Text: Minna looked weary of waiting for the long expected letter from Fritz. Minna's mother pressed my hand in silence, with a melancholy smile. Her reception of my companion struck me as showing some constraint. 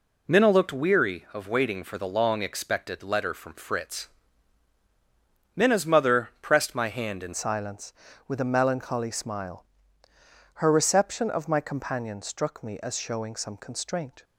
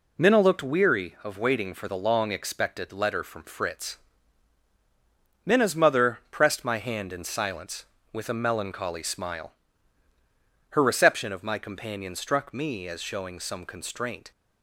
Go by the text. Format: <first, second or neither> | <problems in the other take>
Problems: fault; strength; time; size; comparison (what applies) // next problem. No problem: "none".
second | changes voice at "silence"; from 7.3 s on; 6.9 s long